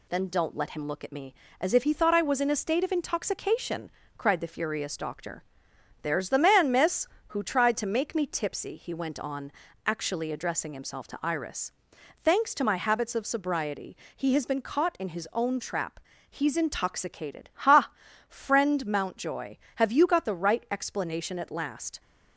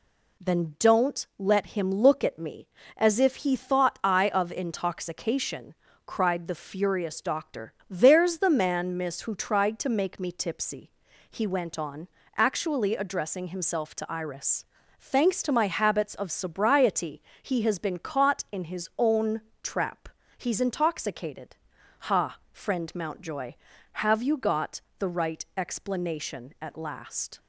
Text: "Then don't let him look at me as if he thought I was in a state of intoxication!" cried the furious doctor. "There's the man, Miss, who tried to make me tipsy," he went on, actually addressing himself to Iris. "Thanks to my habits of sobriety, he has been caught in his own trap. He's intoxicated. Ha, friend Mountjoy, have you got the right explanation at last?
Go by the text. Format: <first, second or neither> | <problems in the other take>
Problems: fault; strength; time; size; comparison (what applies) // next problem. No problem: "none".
first | skips "was in a state"; at 4.2 s // pauses between "own" and "trap"; slight; at 19.3 s; 0.22 s long // pauses between "got" and "the"; slight; at 24.8 s; 0.16 s long